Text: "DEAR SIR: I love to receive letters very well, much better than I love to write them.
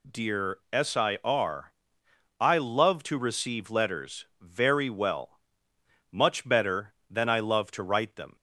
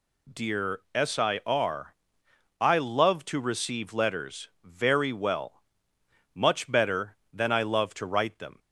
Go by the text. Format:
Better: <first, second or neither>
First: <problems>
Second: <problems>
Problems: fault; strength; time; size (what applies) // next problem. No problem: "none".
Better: neither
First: pauses between "letters" and "very"; slight; at 4.2 s; 0.16 s long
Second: pauses between "letters" and "very"; slight; at 4.4 s; 0.16 s long